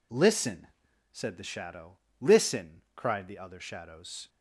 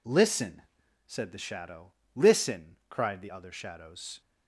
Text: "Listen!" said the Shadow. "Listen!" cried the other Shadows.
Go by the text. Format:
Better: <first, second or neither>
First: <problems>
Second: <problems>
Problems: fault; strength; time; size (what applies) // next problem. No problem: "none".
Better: neither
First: none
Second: none